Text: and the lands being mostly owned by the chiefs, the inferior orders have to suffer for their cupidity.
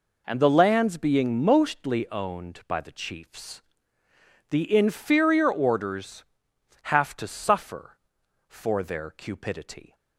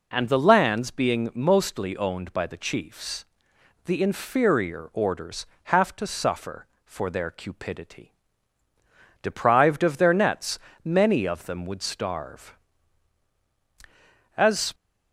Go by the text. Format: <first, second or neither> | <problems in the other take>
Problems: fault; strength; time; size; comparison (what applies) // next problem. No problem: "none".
first | goes on to say "Deprived of their nets many of them would starve As"; strong; from 9.2 s on; 5.5 s long